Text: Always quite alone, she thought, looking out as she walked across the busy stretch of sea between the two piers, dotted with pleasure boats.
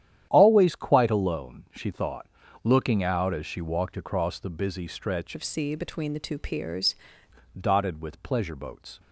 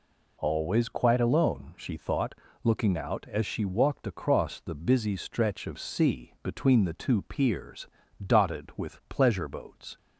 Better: second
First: starts louder than the rest; strong; until 1.3 s; 10.5 dB // changes voice from "of" to "piers"; from 5.3 to 6.9 s; 1.6 s long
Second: none

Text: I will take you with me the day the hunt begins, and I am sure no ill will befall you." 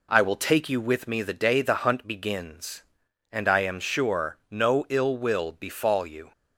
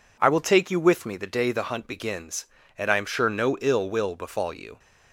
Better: neither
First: none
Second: none

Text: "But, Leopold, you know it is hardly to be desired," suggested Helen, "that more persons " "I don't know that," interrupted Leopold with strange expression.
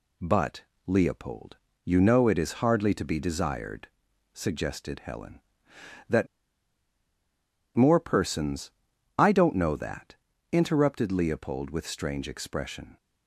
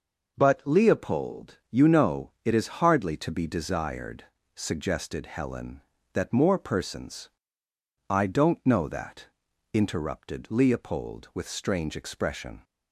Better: second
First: pauses between "that" and "more"; strong; at 6.2 s; 1.4 s long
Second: none

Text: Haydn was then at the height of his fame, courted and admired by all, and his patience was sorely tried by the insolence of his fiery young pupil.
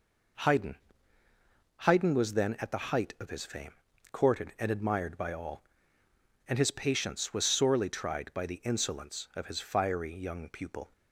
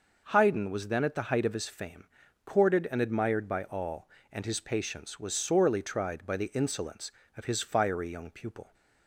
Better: second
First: says "Haydn" twice; at 1.8 s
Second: none

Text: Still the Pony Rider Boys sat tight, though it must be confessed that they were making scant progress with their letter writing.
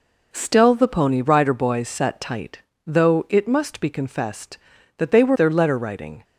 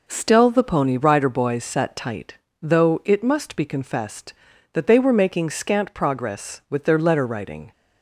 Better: second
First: skips "making scant progress with"; at 5.3 s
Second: none

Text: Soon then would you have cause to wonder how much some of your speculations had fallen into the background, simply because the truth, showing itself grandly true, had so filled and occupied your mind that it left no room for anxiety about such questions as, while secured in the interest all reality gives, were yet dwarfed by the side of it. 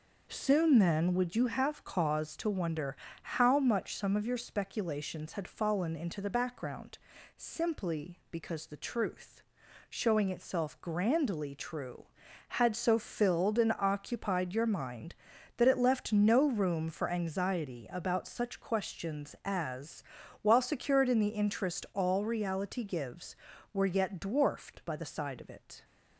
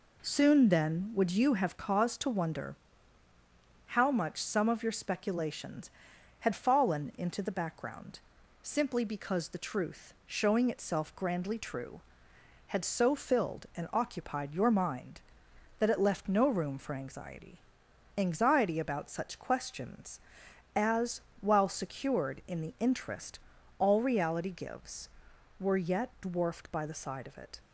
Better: first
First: pauses between "wonder" and "how"; slight; at 2.9 s; 0.26 s long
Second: pauses between "wonder" and "how"; at 2.7 s; 1.1 s long // says "anxiety" twice; at 18.1 s // pauses between "interest" and "all"; at 23.3 s; 0.40 s long

